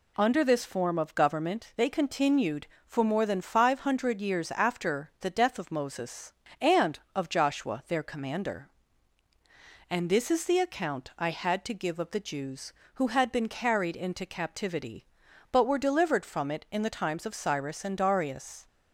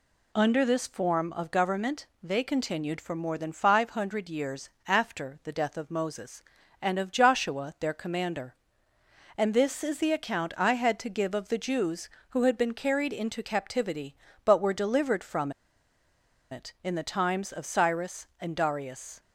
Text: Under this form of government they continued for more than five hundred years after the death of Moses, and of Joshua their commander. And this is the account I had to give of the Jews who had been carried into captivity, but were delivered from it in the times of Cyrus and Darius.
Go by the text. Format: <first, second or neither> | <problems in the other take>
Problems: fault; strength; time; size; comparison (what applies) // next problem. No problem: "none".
first | pauses between "government" and "they"; slight; at 2.0 s; 0.16 s long // pauses between "years" and "after"; slight; at 4.7 s; 0.16 s long // pauses between "from" and "it"; at 15.5 s; 1.0 s long